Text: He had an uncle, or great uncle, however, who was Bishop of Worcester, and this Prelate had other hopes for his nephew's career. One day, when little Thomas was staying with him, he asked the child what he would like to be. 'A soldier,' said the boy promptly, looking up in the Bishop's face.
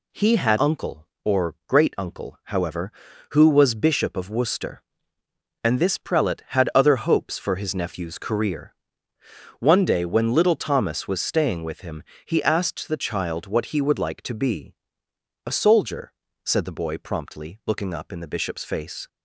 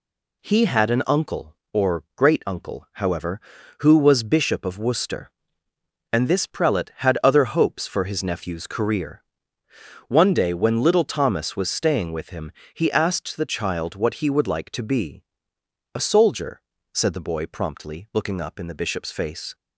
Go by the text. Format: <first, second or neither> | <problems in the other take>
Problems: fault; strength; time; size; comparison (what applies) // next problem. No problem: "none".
second | skips "an"; at 0.5 s